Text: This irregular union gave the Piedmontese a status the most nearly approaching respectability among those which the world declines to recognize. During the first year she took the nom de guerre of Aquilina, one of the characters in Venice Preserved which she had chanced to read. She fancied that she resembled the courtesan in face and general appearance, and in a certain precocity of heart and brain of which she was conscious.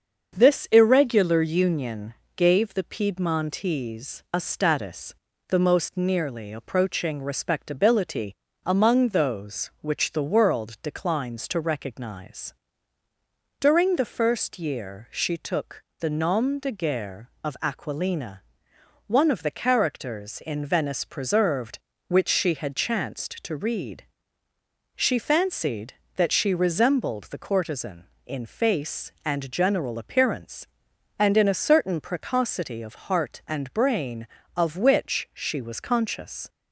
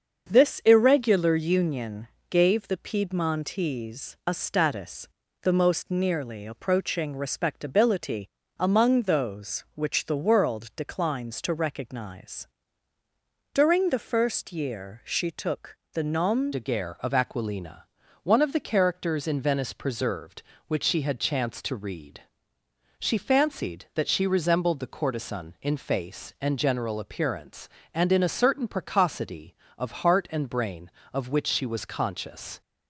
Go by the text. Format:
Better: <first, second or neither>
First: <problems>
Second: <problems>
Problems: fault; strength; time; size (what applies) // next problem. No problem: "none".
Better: first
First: starts louder than the rest; until 1.4 s; 7 dB // pauses between "union" and "gave"; slight; at 2.1 s; 0.22 s long // pauses between "status" and "the"; slight; at 5.1 s; 0.36 s long // pauses between "respectability" and "among"; slight; at 8.3 s; 0.32 s long // pauses between "took" and "the"; slight; at 15.8 s; 0.16 s long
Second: starts louder than the rest; until 1.3 s; 7 dB // pauses between "union" and "gave"; slight; at 2.0 s; 0.22 s long // pauses between "status" and "the"; slight; at 5.0 s; 0.36 s long // pauses between "respectability" and "among"; slight; at 8.2 s; 0.32 s long // pauses between "took" and "the"; slight; at 15.7 s; 0.16 s long // changes voice at "de"; from 16.5 s on; 16.1 s long